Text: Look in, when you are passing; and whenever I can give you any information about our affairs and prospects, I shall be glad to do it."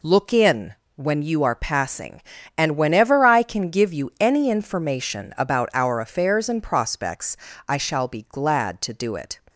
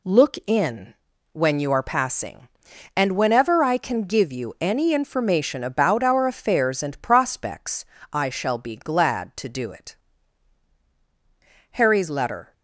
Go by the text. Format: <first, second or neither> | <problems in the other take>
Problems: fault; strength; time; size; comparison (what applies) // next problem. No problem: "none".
first | goes on to say "Harry's letter"; noticeable; from 11.7 s on; 0.82 s long